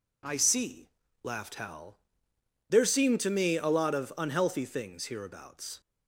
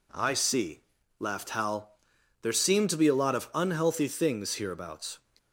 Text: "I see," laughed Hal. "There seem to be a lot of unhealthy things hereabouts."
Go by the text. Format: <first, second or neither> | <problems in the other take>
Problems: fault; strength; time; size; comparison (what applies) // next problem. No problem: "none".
second | says "me" for "be"; at 3.2 s